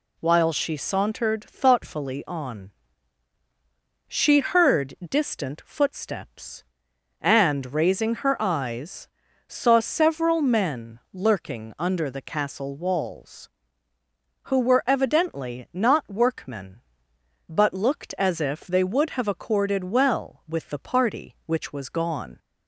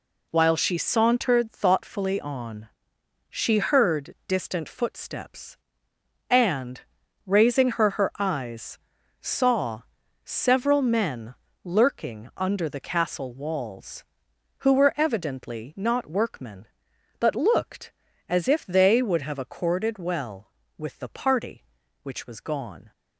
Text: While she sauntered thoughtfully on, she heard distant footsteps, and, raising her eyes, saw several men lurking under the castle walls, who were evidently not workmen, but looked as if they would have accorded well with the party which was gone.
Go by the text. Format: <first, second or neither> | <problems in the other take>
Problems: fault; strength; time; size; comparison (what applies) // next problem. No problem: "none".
first | says "her" twice; at 7.9 s // pauses between "saw" and "several"; at 9.8 s; 0.42 s long // pauses between "men" and "lurking"; slight; at 11.3 s; 0.28 s long